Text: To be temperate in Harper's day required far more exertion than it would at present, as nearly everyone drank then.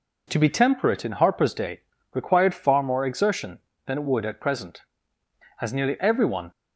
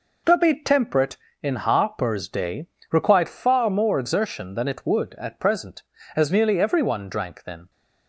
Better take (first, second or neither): second